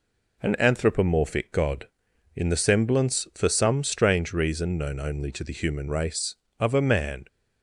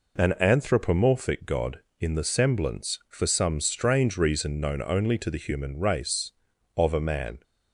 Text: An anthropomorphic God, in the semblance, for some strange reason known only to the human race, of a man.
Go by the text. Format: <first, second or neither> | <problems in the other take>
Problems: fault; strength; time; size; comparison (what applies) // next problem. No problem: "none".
neither | none